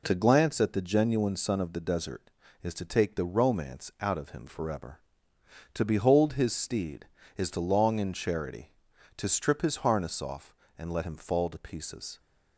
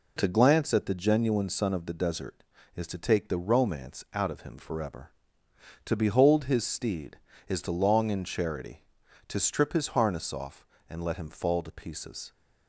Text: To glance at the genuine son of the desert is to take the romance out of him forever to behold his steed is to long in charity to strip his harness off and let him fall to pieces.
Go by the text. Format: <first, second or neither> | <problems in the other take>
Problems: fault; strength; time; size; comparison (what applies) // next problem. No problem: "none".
neither | none